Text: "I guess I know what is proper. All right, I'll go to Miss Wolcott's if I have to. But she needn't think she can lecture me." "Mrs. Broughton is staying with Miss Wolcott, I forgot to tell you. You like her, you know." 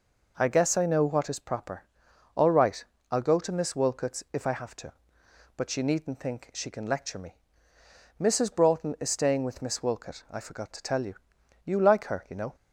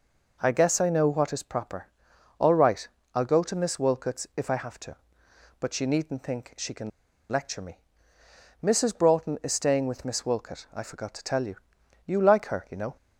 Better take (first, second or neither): first